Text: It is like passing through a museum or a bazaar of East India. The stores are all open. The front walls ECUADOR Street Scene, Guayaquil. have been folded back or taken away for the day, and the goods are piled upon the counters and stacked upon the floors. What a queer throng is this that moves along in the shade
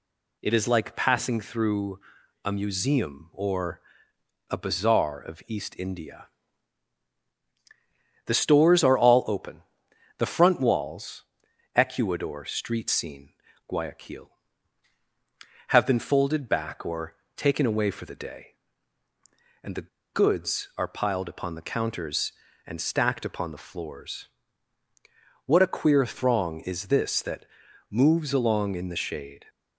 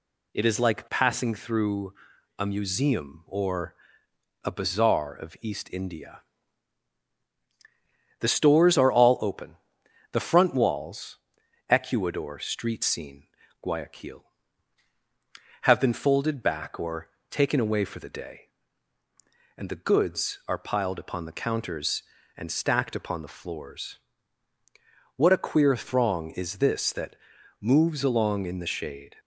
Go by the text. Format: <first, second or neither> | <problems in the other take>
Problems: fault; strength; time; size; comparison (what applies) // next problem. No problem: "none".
second | pauses between "through" and "a"; noticeable; at 1.9 s; 0.46 s long; noticeable in the second // pauses between "or" and "a"; noticeable; at 3.8 s; 0.70 s long; noticeable in the second // pauses between "walls" and "ECUADOR"; noticeable; at 11.2 s; 0.52 s long; noticeable in the second // pauses between "or" and "taken"; slight; at 17.1 s; 0.22 s long; slight in the second // pauses between "the" and "goods"; slight; at 19.8 s; 0.25 s long // pauses between "that" and "moves"; at 27.4 s; 0.42 s long; also in the second